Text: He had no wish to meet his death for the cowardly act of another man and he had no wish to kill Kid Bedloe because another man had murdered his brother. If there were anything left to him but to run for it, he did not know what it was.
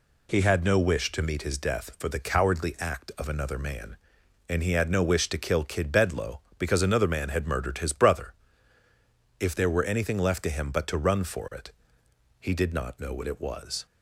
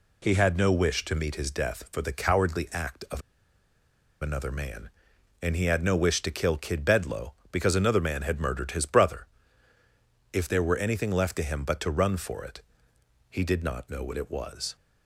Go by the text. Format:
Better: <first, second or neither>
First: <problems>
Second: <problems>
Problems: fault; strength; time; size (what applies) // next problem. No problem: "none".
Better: first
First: none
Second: pauses between "of" and "another"; at 3.2 s; 1.0 s long